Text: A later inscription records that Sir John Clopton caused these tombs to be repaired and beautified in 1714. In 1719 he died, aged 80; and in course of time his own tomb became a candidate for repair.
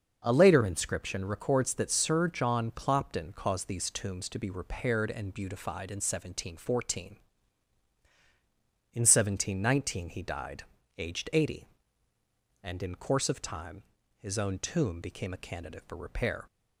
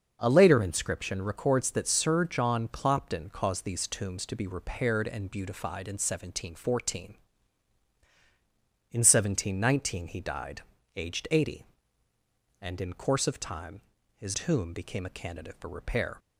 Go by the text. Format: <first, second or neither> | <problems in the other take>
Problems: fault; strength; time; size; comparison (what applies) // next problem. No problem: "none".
first | starts louder than the rest; until 1.2 s; 6 dB; also in the first // pauses between "time" and "his"; slight; at 13.8 s; 0.34 s long; slight in the first // skips "own"; at 14.3 s